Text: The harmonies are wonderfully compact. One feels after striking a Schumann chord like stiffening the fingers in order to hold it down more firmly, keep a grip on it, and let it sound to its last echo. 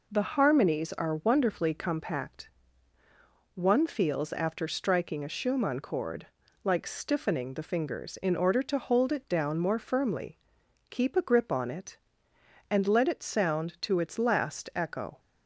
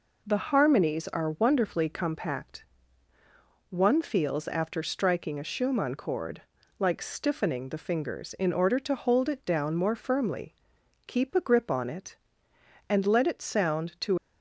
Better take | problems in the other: first | pauses between "chord" and "like"; slight; at 6.4 s; 0.36 s long; slight in the first // stops before "its last echo"; at 14.1 s

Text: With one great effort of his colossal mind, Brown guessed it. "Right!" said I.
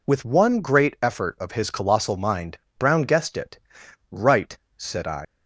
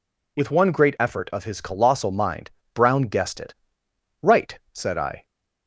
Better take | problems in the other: second | leaves "I" unfinished; at 5.2 s; 125 ms

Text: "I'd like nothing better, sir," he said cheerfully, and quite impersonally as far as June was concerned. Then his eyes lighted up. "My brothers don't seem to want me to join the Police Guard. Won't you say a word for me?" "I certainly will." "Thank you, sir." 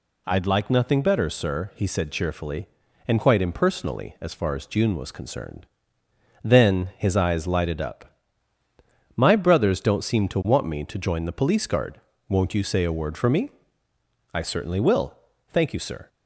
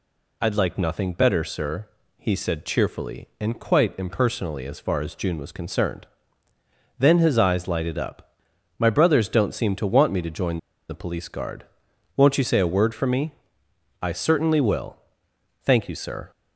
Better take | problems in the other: first | pauses between "join" and "the"; slight; at 10.5 s; 0.32 s long

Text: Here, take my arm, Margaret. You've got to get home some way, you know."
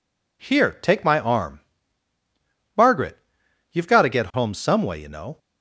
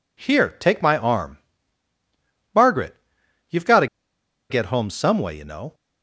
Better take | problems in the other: first | pauses between "to" and "get"; noticeable; at 3.8 s; 0.63 s long

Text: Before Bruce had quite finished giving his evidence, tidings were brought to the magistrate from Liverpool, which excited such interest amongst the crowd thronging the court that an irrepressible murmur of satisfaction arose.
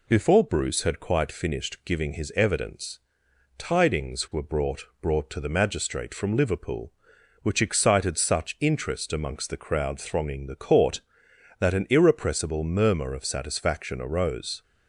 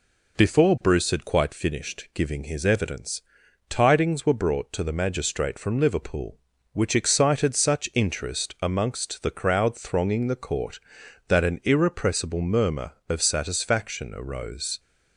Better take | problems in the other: second | says "brought" twice; at 5.0 s

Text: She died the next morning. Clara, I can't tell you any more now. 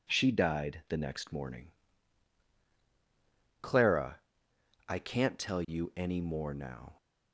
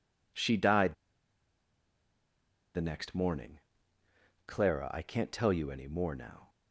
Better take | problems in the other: first | pauses between "died" and "the"; strong; at 0.9 s; 1.8 s long

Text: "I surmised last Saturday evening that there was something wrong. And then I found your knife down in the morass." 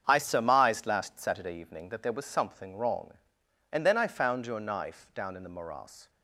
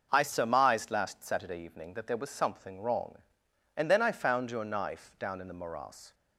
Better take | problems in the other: second | gets quieter; strong; throughout; 9.5 dB

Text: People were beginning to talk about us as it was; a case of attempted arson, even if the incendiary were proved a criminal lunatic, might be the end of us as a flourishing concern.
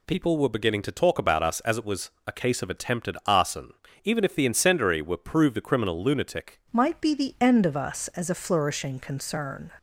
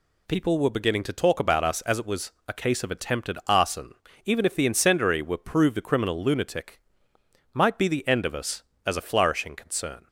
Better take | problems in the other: second | changes voice at "might"; from 6.7 s on; 3.0 s long

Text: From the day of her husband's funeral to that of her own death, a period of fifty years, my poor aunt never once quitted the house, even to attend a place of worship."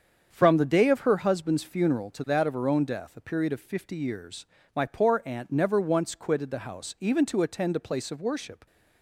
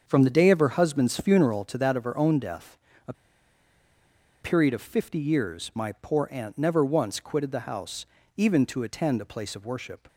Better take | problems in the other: first | starts louder than the rest; strong; until 1.0 s; 7 dB; strong in the first // pauses between "a" and "period"; strong; at 3.1 s; 1.2 s long

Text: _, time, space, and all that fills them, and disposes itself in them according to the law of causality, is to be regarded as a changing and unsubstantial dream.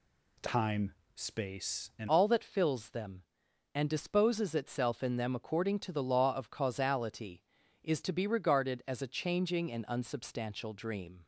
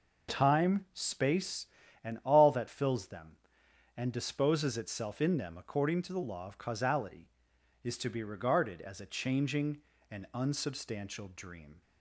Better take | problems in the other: second | changes voice at "all"; from 2.0 s on; 9.2 s long

